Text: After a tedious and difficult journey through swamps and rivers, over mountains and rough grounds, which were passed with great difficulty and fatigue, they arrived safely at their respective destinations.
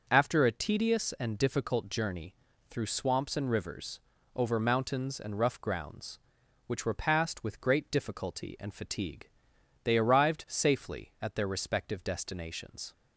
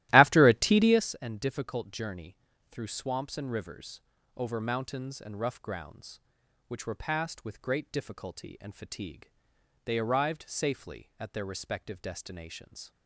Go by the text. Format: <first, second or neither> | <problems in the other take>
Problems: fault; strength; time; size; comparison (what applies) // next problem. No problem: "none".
first | starts louder than the rest; strong; until 1.1 s; 16 dB // pauses between "journey" and "through"; slight; at 2.3 s; 0.35 s long; slight in the first